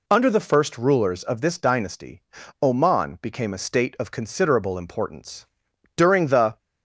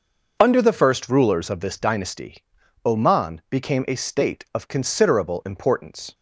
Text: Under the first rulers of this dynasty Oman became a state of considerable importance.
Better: second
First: pauses between "dynasty" and "Oman"; at 2.2 s; 0.40 s long // goes on to say "During the"; noticeable; from 5.9 s on; 0.62 s long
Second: pauses between "dynasty" and "Oman"; at 2.4 s; 0.40 s long

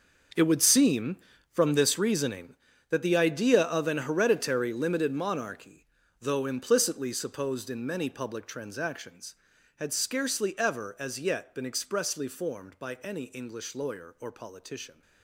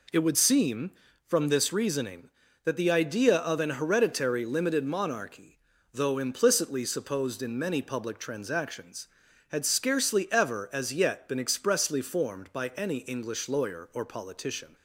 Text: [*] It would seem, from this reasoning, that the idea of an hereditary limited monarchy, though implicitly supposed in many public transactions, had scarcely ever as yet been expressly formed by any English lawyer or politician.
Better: second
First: gets quieter; strong; throughout; 14.5 dB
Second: none

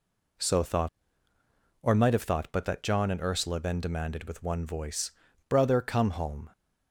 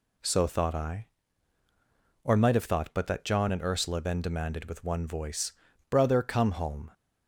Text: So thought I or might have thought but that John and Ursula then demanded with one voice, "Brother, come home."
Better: second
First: skips "I"; at 1.3 s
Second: none

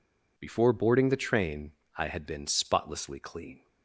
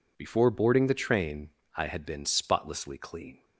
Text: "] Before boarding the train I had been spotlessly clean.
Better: neither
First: pauses between "train" and "I"; slight; at 1.7 s; 0.24 s long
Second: pauses between "train" and "I"; slight; at 1.4 s; 0.26 s long

